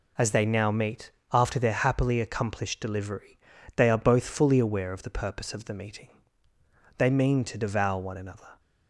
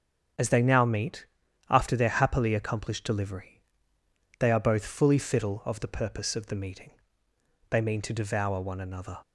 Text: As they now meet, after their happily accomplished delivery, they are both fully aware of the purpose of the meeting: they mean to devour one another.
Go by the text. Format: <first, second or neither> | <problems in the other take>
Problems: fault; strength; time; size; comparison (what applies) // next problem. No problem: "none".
first | starts louder than the rest; strong; until 1.8 s; 7.5 dB // says "fiddle" for "aware"; at 5.1 s